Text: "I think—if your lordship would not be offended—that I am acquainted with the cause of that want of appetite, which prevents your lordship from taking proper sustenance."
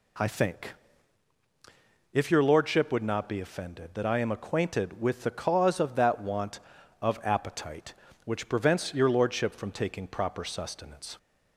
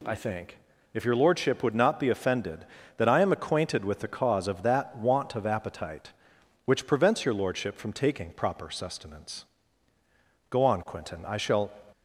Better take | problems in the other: first | goes on to say "Go on Quentin I shall"; noticeable; from 10.4 s on; 1.2 s long

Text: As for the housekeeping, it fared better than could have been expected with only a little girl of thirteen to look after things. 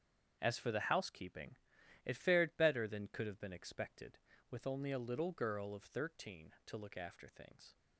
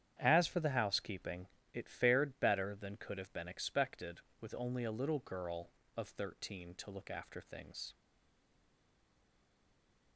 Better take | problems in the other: first | starts louder than the rest; strong; until 1.2 s; 9.5 dB; strong in the first // stays silent after the last word; from 7.9 s on; 2.2 s long

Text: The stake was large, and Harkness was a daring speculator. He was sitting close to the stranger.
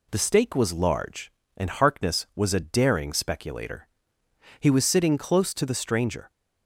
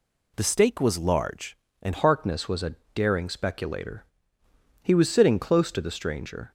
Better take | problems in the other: first | changes voice at "Harkness"; from 1.9 s on; 4.6 s long // pauses between "a" and "daring"; slight; at 2.7 s; 0.20 s long

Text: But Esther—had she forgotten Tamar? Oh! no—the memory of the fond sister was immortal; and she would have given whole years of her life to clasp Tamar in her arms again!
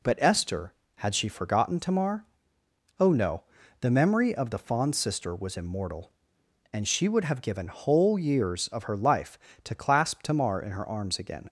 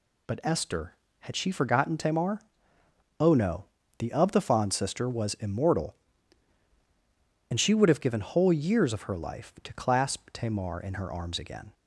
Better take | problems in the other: first | skips "memory"; at 4.1 s

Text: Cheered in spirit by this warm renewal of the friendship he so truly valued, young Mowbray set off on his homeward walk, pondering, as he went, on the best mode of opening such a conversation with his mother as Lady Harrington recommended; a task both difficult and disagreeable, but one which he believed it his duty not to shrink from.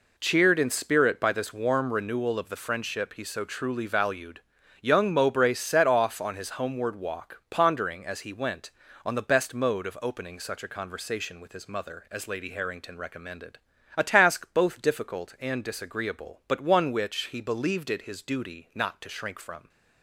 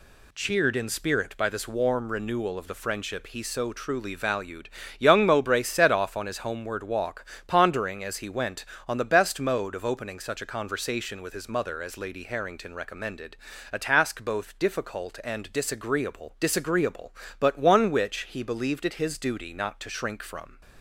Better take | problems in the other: first | says "disagreeable" twice; at 16.3 s

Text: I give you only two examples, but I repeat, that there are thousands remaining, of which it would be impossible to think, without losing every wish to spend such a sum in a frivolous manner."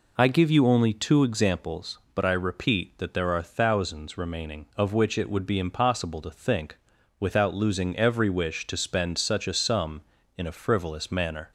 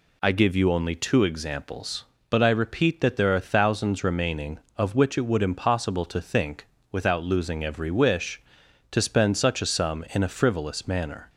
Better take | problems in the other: first | skips "be"; at 5.4 s

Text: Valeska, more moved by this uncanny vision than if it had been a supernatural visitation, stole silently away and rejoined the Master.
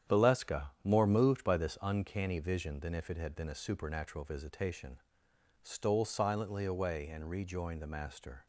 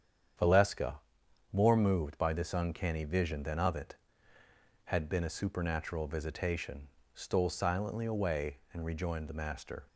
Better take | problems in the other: first | starts louder than the rest; strong; until 1.9 s; 8.5 dB; strong in the first // says "of" for "if"; at 3.5 s

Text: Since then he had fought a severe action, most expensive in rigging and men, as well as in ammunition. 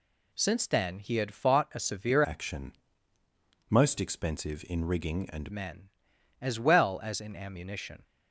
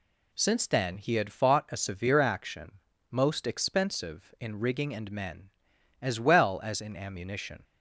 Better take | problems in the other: second | changes voice from "action" to "and"; from 2.2 to 5.5 s; 3.3 s long

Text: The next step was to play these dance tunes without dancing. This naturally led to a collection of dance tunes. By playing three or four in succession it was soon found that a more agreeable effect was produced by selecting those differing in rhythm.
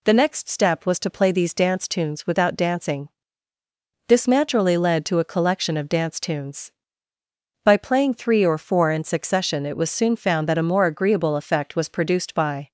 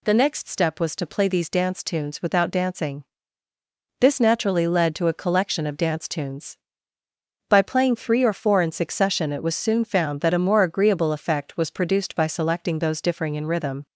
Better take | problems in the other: second | stops before "selecting those differing in rhythm"; at 12.6 s

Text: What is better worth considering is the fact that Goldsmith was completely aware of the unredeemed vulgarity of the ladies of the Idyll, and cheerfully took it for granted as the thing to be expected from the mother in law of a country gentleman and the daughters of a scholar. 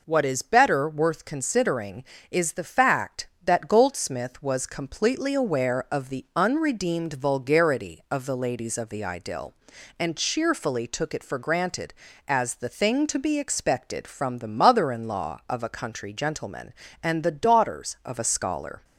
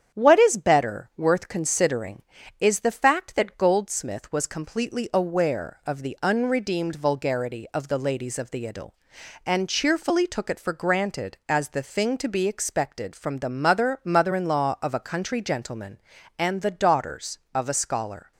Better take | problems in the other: first | starts louder than the rest; strong; until 1.2 s; 8.5 dB // says "mother" twice; at 14.0 s

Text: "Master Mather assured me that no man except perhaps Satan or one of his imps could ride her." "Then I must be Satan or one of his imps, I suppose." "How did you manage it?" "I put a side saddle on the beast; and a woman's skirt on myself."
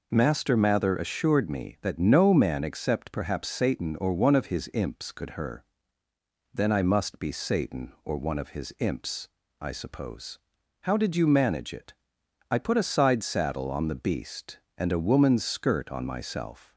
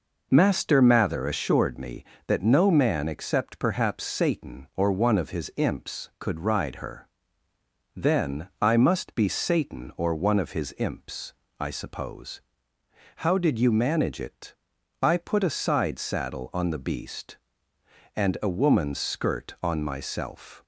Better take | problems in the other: second | skips "ride"; at 5.3 s

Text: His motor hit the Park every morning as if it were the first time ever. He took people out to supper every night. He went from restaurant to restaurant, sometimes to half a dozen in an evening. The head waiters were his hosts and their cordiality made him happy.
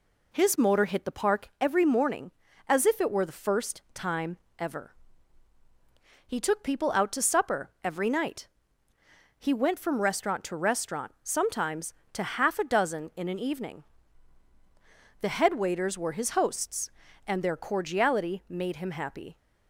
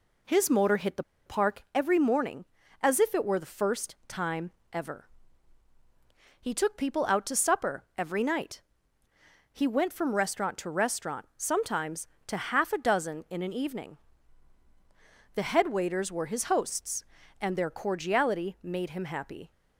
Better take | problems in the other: first | pauses between "the" and "Park"; slight; at 1.0 s; 0.22 s long // pauses between "time" and "ever"; slight; at 4.4 s; 0.22 s long; slight in the first

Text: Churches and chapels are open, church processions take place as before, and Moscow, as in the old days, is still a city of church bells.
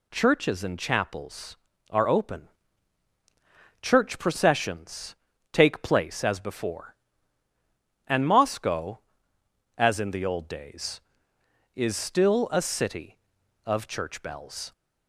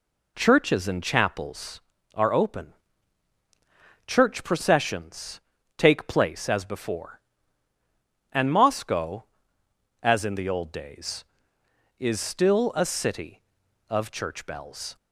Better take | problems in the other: first | starts louder than the rest; slight; until 1.8 s; 3 dB // pauses between "processions" and "take"; slight; at 5.4 s; 0.36 s long; slight in the first

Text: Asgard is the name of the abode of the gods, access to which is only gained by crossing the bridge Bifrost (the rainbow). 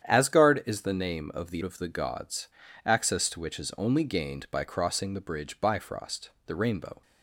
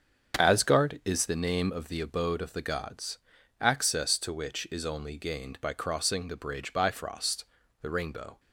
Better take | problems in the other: second | starts louder than the rest; strong; until 1.0 s; 9 dB; strong in the second // skips "abode"; at 1.6 s

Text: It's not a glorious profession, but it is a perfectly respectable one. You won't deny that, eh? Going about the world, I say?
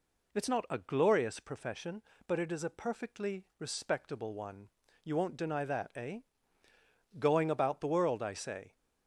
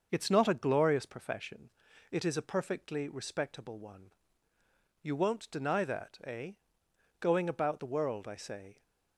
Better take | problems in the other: first | starts louder than the rest; until 1.1 s; 6 dB // skips "but"; at 1.8 s

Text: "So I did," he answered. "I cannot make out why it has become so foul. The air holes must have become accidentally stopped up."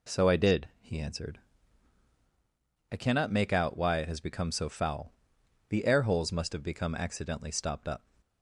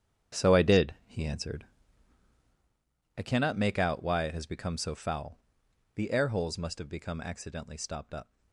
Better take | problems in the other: first | gets quieter; strong; throughout; 11 dB

